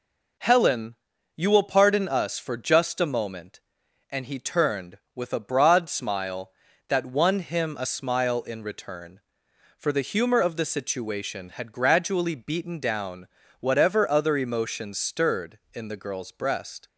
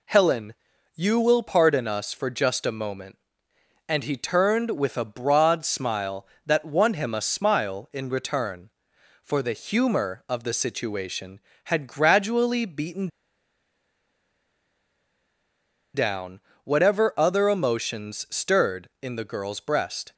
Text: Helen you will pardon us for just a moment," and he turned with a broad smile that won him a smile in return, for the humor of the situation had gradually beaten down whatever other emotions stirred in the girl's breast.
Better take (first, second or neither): first